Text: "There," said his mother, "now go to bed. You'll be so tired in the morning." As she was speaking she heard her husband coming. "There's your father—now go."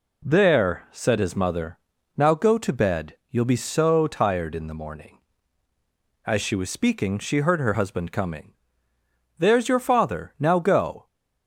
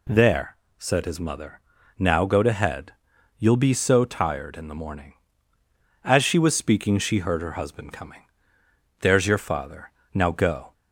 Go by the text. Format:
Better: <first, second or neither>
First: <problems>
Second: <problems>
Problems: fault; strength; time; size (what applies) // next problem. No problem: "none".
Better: first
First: none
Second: says "head" for "bed"; at 2.5 s